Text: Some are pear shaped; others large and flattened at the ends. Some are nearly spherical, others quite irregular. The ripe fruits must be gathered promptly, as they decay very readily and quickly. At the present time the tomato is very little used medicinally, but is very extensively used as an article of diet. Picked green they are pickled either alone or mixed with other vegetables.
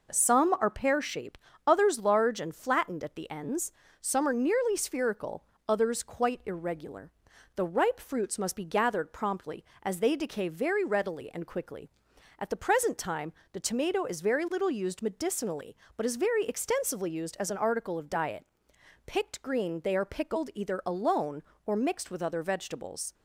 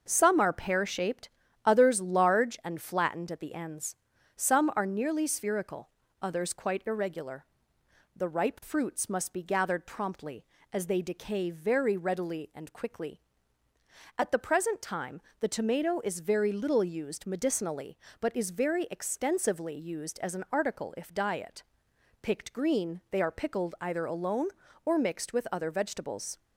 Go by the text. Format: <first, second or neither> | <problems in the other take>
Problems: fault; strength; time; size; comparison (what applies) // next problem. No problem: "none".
first | starts louder than the rest; until 1.0 s; 6 dB // pauses between "time" and "the"; slight; at 15.1 s; 0.18 s long; slight in the first // says "if" for "of"; at 20.9 s